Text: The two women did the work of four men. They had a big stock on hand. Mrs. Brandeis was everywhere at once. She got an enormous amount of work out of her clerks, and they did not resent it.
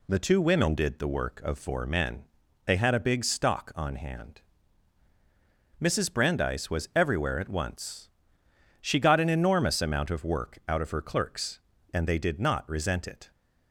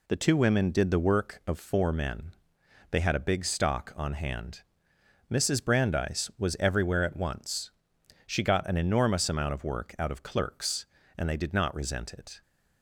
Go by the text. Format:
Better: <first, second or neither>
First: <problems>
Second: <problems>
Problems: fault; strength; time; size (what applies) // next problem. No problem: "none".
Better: first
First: none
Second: skips "her"; at 10.2 s